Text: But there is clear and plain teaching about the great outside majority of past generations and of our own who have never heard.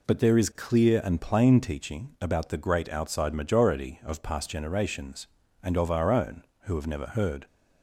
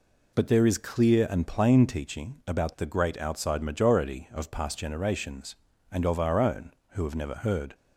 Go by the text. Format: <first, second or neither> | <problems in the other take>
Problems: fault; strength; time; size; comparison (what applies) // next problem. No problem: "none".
neither | none